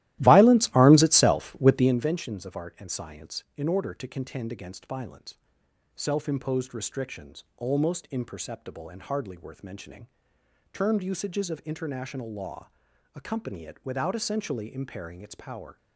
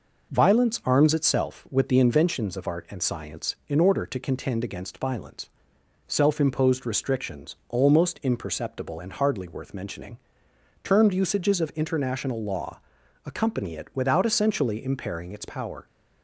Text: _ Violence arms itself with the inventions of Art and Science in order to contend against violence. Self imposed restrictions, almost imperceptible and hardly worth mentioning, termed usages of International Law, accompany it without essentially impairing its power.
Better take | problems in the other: second | starts louder than the rest; strong; until 2.0 s; 15.5 dB

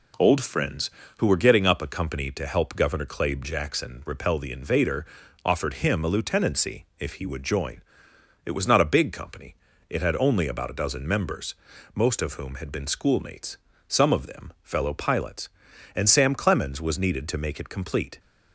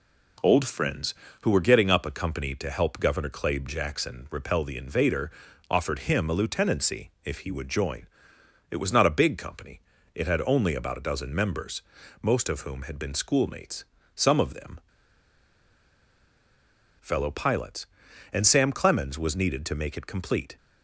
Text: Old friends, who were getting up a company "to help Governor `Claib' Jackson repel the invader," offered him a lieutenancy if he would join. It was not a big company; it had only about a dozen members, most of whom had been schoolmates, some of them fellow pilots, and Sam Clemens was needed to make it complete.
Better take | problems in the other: first | pauses between "them" and "fellow"; strong; at 14.7 s; 2.2 s long

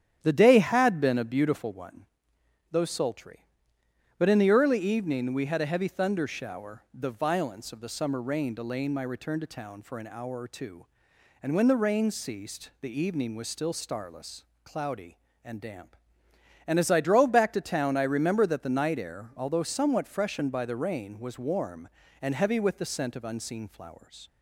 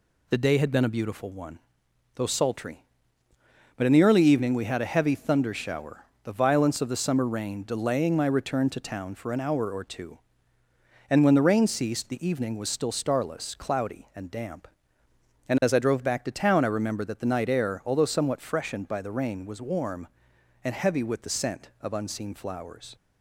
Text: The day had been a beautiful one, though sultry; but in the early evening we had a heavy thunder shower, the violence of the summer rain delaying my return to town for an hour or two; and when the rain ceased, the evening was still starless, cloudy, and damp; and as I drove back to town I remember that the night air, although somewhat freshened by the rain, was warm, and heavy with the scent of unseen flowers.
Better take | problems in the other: second | starts louder than the rest; strong; until 1.9 s; 10 dB

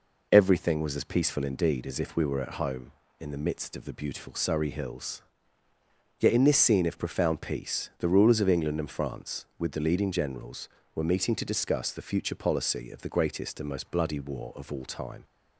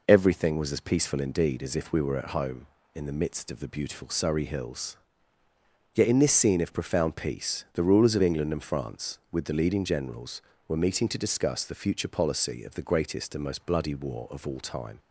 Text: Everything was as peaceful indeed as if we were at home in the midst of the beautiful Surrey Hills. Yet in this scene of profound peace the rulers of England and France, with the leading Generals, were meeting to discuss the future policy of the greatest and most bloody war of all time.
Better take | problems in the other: neither | none

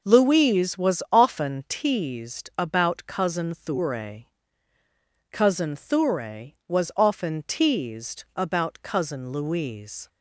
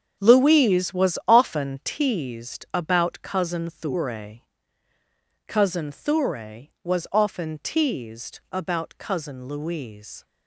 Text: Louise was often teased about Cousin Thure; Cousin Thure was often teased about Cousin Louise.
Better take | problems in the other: first | gets quieter; strong; throughout; 10 dB

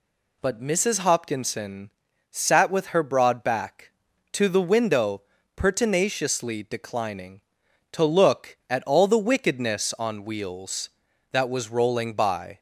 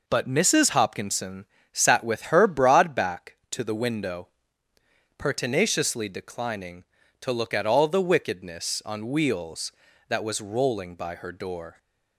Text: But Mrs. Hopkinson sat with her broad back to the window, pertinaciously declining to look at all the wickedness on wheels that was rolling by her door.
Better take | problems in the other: second | pauses between "Hopkinson" and "sat"; at 1.9 s; 0.40 s long; slight in the second // stops before "her door"; at 12.5 s

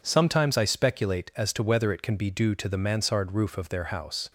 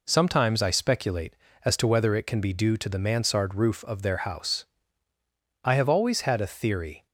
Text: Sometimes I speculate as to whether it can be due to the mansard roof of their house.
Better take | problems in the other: first | goes on to say "I have always had a theory"; from 5.6 s on; 1.4 s long

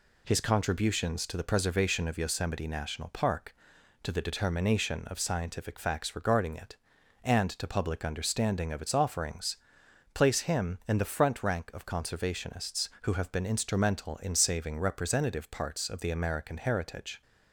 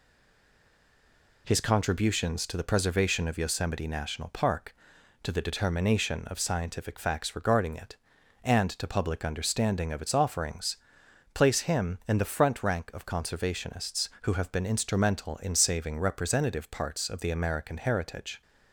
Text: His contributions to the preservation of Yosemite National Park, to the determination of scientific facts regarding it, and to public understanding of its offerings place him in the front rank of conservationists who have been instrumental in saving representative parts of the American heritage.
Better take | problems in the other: first | stays silent before the first word; noticeable; until 1.4 s; 1.4 s long // pauses between "offerings" and "place"; noticeable; at 10.7 s; 0.60 s long; noticeable in the first

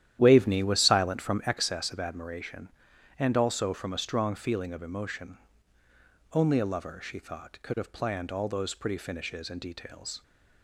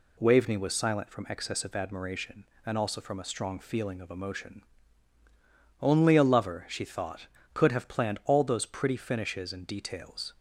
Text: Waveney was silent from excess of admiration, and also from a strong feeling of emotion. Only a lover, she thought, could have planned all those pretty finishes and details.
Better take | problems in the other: second | starts louder than the rest; strong; until 1.7 s; 11.5 dB

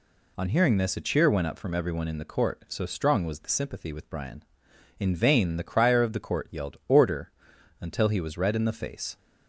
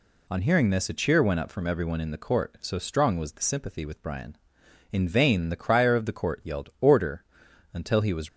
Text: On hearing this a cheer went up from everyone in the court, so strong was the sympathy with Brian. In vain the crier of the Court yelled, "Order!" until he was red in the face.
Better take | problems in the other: first | stops before "red in the face"; at 8.2 s

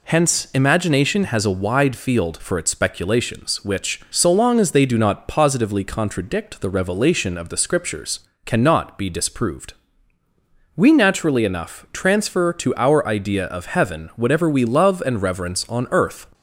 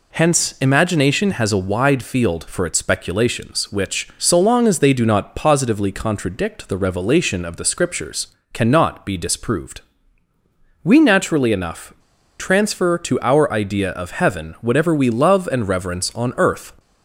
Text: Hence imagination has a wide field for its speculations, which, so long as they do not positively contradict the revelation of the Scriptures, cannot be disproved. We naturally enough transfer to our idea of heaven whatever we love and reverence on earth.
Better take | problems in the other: first | pauses between "enough" and "transfer"; at 11.9 s; 0.45 s long

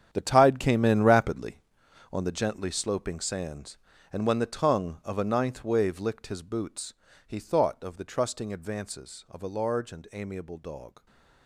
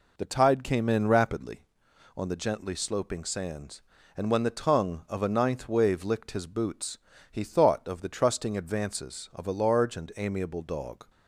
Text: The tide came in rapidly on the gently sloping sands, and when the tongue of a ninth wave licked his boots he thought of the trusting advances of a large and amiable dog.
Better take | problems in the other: second | gets quieter; strong; throughout; 13 dB // pauses between "boots" and "he"; slight; at 6.9 s; 0.34 s long; slight in the second

